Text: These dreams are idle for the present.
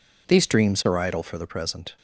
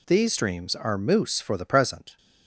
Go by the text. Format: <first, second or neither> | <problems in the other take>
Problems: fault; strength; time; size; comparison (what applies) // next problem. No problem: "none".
first | says "moose" for "idle"; at 0.9 s